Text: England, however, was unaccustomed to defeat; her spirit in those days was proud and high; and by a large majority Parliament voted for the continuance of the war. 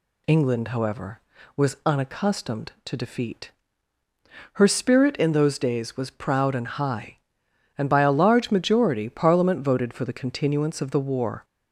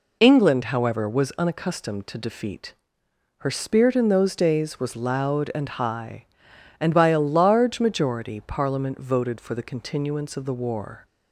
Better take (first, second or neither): first